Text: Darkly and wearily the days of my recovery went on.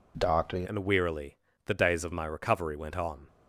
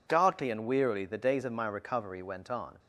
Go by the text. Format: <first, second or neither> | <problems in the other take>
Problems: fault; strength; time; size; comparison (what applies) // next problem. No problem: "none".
second | changes voice at "and"; from 0.6 s on; 2.6 s long // pauses between "wearily" and "the"; slight; at 1.3 s; 0.28 s long